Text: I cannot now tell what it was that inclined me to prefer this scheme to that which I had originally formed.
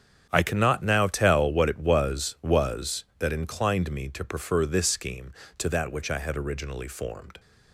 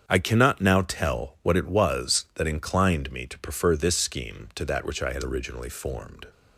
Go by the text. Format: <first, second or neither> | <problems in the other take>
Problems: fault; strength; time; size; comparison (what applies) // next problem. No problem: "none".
second | starts louder than the rest; strong; until 1.3 s; 8 dB; strong in the second // says "was" twice; at 2.4 s